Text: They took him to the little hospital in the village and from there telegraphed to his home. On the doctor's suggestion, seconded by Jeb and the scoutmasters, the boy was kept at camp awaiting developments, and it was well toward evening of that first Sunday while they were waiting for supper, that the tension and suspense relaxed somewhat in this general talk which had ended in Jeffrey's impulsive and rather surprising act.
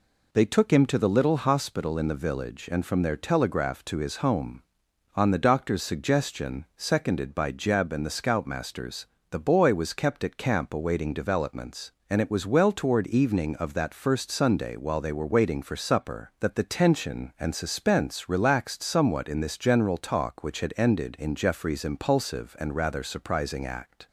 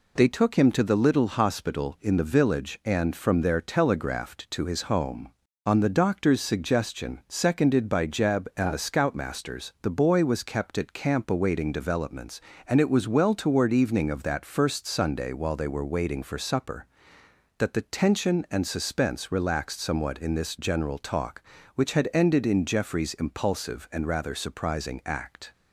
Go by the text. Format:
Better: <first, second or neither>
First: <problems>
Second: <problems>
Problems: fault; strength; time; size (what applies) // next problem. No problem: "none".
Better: neither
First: none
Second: none